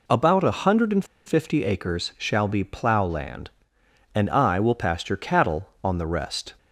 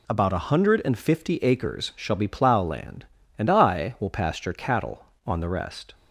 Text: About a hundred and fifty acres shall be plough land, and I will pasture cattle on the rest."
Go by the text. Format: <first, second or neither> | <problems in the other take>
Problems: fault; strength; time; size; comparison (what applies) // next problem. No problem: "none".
second | pauses between "and" and "fifty"; slight; at 1.0 s; 0.22 s long